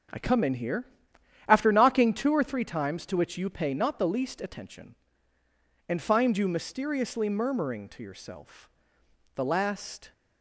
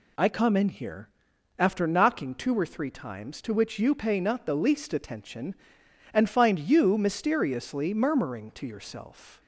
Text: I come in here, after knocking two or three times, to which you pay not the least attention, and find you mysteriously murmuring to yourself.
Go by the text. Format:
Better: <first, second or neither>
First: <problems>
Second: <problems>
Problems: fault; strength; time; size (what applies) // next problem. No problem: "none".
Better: second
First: starts louder than the rest; until 1.7 s; 6.5 dB // goes on to say "The last"; noticeable; from 9.3 s on; 0.78 s long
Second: none